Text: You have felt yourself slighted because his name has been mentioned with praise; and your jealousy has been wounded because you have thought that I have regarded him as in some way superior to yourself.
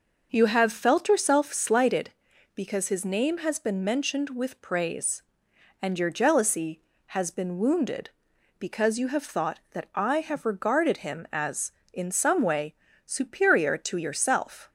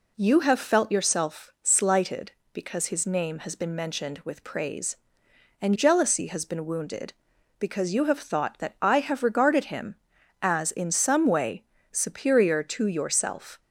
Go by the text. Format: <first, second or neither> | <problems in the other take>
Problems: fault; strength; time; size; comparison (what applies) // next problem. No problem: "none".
first | skips "your"; at 5.7 s // pauses between "way" and "superior"; slight; at 11.6 s; 0.28 s long; slight in the first